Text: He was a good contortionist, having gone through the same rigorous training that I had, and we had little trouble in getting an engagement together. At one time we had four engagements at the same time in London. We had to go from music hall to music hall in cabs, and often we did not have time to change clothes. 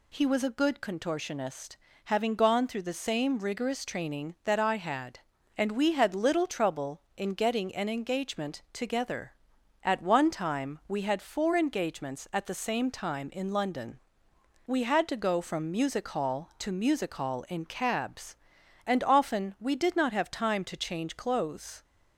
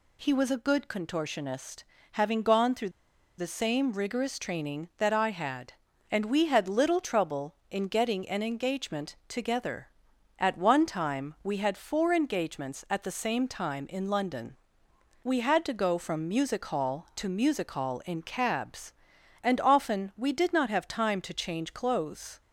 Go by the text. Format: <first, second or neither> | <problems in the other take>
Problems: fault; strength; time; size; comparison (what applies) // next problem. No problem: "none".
first | pauses between "through" and "the"; noticeable; at 2.8 s; 0.48 s long